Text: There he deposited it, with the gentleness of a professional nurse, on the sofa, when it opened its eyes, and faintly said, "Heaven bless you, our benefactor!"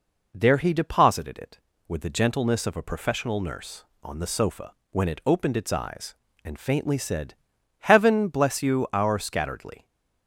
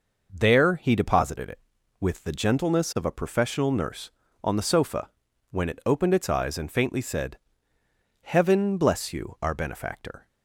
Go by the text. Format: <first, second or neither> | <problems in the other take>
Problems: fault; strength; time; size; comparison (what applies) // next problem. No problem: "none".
second | says "scatteredly" for "benefactor"; at 9.1 s